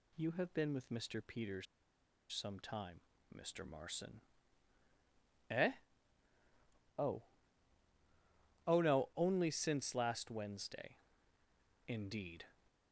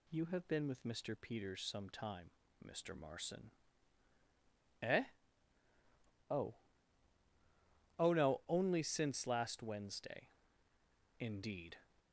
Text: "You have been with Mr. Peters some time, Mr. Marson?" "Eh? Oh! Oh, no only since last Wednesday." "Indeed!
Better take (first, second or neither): second